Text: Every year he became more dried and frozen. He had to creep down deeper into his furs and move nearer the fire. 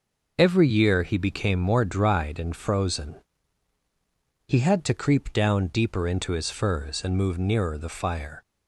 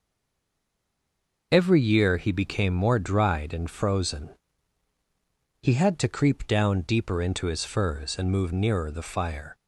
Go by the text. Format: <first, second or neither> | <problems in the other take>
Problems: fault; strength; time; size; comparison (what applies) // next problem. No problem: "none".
first | stays silent before the first word; noticeable; until 1.5 s; 1.5 s long